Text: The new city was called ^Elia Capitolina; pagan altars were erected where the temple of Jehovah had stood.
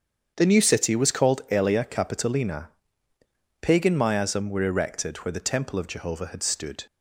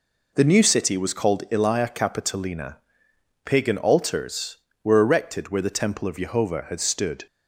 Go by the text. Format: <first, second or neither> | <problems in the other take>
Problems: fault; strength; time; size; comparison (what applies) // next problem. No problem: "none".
second | starts louder than the rest; strong; until 1.3 s; 7.5 dB // says "miasm" for "altars"; at 3.9 s